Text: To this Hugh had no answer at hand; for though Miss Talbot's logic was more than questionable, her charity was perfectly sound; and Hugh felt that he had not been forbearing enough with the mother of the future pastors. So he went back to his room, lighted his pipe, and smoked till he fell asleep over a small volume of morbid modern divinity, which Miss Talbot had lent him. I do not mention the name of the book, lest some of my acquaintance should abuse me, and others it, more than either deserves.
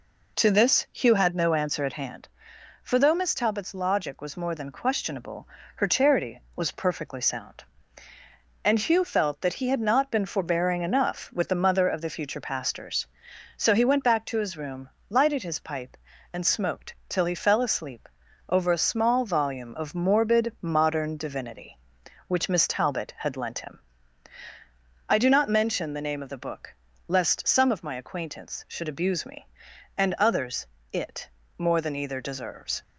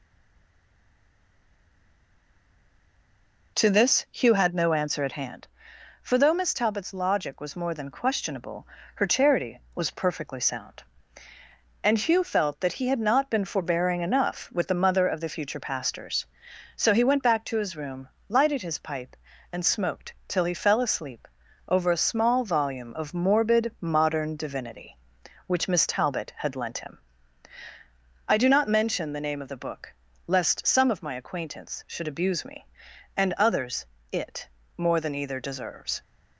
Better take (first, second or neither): first